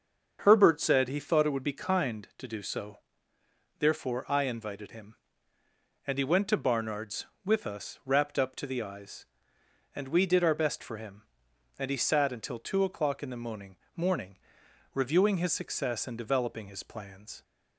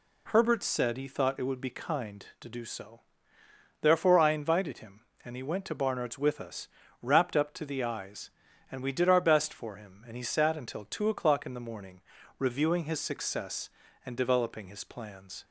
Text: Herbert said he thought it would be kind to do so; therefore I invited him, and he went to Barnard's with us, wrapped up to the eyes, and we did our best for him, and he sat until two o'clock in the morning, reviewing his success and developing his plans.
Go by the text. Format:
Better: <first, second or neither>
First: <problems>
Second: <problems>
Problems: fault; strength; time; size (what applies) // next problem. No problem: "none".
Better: second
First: starts louder than the rest; until 1.4 s; 6.5 dB // says "morning" twice; at 13.9 s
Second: none